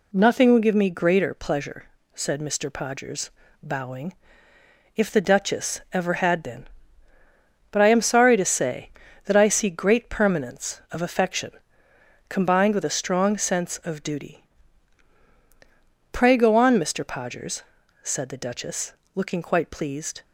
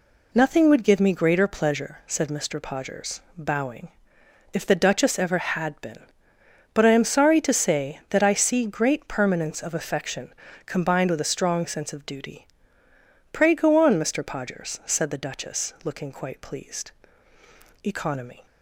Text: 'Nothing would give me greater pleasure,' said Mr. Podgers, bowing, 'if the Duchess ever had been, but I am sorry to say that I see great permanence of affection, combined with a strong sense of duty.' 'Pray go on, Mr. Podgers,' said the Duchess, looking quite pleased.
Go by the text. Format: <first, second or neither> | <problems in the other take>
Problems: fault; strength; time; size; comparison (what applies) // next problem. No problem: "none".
first | goes on to say "Economy"; noticeable; from 17.8 s on; 0.62 s long